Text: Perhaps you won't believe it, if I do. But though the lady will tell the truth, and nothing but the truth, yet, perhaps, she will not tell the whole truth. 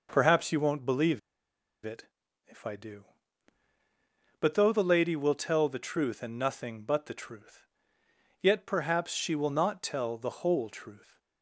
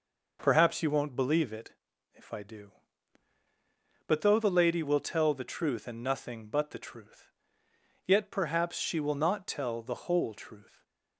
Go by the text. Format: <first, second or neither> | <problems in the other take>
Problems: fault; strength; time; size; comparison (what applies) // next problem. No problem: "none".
second | pauses between "believe" and "it"; noticeable; at 1.1 s; 0.65 s long